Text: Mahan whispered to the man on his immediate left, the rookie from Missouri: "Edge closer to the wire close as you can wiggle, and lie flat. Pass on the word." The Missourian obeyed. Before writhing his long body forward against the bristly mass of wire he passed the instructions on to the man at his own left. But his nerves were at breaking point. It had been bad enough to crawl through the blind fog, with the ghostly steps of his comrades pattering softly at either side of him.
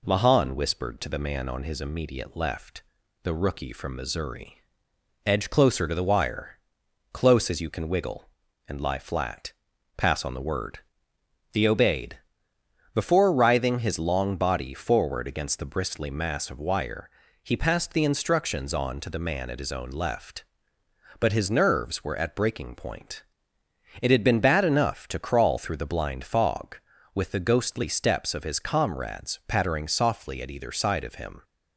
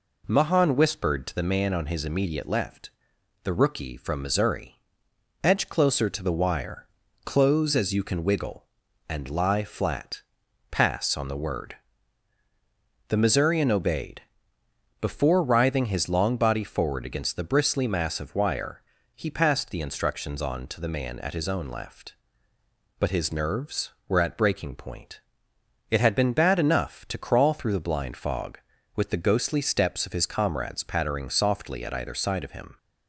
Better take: second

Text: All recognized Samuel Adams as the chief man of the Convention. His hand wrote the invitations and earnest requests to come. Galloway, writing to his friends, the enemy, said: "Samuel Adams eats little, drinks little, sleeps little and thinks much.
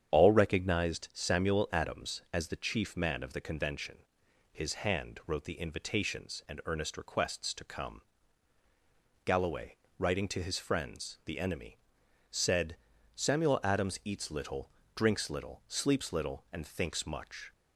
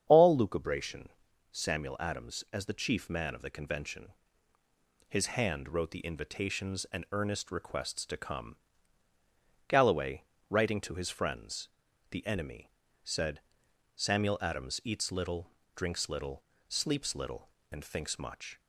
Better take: first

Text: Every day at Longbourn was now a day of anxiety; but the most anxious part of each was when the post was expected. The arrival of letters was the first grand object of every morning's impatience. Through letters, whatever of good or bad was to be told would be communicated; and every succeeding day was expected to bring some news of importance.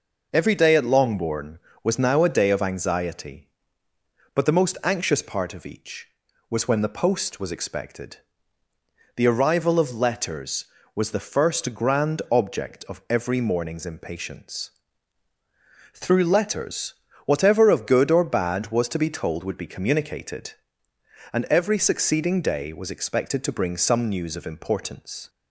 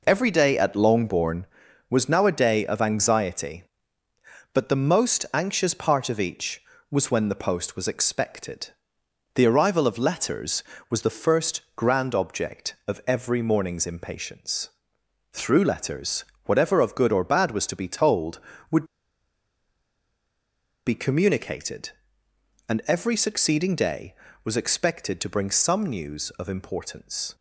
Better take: first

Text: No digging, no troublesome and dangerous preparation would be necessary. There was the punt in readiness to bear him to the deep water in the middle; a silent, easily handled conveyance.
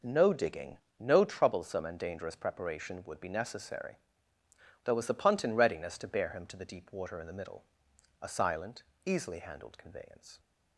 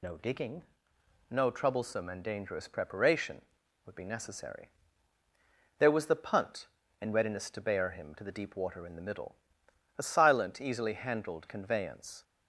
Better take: first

